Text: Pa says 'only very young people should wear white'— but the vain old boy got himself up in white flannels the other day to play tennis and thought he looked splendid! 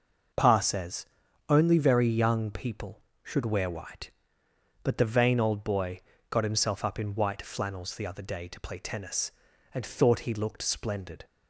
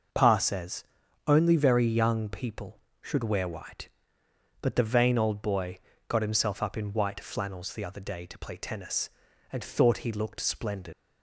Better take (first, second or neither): first